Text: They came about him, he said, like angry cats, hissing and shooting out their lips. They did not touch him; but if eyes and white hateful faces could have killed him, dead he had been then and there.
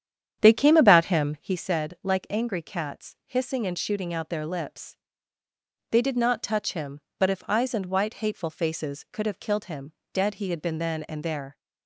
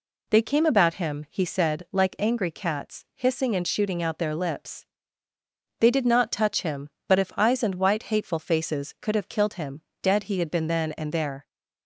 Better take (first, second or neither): second